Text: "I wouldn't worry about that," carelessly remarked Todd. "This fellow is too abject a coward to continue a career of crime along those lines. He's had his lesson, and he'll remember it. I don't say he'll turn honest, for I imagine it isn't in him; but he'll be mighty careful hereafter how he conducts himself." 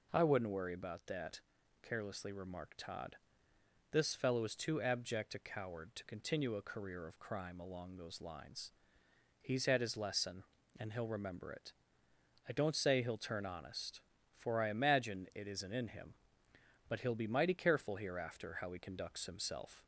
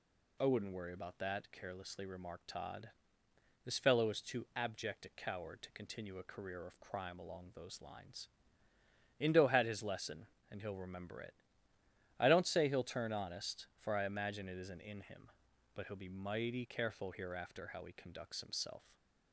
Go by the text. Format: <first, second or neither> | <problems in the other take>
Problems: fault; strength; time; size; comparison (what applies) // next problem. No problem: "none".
first | says "Indo" for "He's"; at 9.1 s // stays silent after the last word; slight; from 18.7 s on; 0.6 s long